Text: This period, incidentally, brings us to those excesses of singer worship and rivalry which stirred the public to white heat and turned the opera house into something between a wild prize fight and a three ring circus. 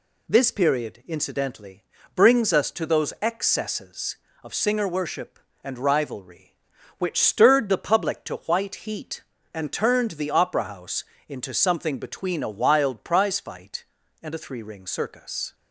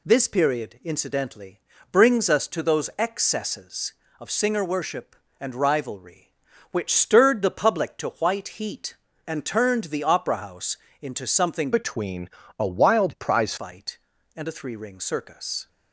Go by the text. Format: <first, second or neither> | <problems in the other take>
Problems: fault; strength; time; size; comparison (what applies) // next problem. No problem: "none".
first | pauses between "house" and "into"; slight; at 10.7 s; 0.28 s long; slight in the first // changes voice from "between" to "prize"; from 11.7 to 13.5 s; 1.8 s long // pauses between "between" and "a"; slight; at 12.2 s; 0.30 s long